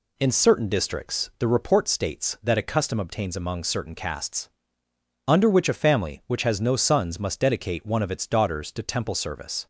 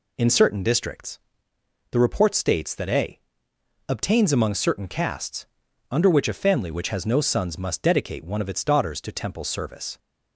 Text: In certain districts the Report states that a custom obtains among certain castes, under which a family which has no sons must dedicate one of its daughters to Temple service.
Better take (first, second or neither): first